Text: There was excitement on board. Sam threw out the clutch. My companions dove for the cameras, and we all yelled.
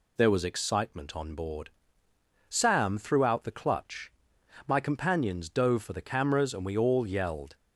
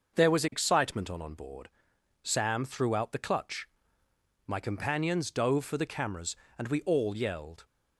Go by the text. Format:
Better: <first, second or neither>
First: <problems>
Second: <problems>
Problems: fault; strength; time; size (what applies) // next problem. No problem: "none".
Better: first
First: none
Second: starts louder than the rest; noticeable; until 1.2 s; 6 dB // says "on" twice; at 1.2 s